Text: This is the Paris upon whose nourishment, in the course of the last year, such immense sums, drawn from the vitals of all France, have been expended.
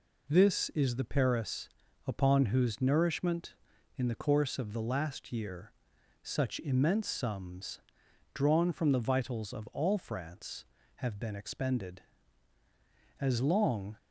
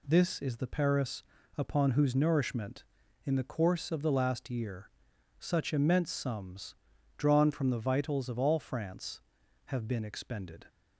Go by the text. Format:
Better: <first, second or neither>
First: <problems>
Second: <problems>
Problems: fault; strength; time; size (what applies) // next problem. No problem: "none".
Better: second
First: pauses between "Paris" and "upon"; at 1.6 s; 0.38 s long // goes on to say "As long"; noticeable; from 13.2 s on; 0.76 s long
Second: pauses between "Paris" and "upon"; slight; at 1.2 s; 0.34 s long